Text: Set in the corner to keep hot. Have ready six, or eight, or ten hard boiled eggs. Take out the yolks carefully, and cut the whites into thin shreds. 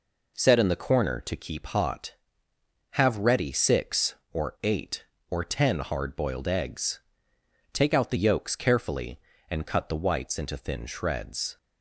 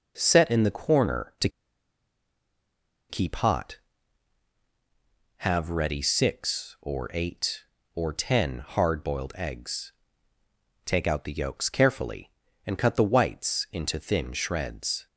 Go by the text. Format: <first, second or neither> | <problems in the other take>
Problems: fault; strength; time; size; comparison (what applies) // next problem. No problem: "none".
first | pauses between "to" and "keep"; strong; at 1.4 s; 1.6 s long